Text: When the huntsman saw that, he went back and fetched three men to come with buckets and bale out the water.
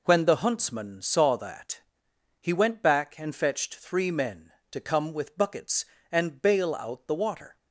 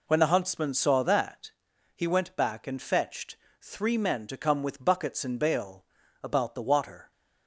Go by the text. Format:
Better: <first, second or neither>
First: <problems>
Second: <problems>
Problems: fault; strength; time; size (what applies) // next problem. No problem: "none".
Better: first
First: none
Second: pauses between "fetched" and "three"; slight; at 3.3 s; 0.24 s long // says "about" for "out"; at 6.2 s